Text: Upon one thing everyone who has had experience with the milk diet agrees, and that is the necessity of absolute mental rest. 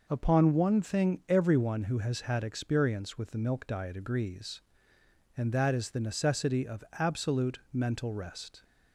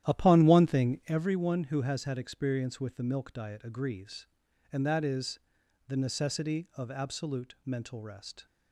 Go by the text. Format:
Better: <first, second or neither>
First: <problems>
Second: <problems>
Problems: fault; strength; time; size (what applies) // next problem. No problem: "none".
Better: first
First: none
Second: starts louder than the rest; strong; until 1.2 s; 11.5 dB // pauses between "is" and "the"; noticeable; at 5.3 s; 0.48 s long